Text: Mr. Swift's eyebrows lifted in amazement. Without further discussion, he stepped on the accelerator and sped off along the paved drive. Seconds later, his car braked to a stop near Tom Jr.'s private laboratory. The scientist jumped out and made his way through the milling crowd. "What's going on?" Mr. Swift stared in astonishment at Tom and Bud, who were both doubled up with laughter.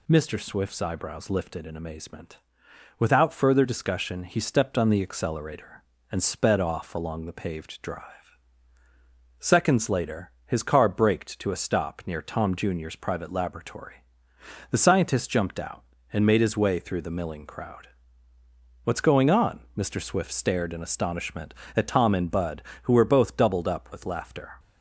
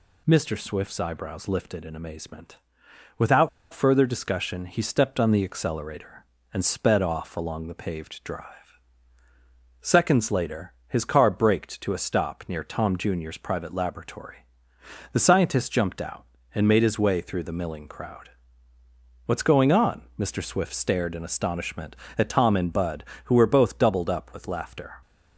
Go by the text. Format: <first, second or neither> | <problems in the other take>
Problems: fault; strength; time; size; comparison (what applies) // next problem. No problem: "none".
first | pauses between "Without" and "further"; slight; at 3.4 s; 0.23 s long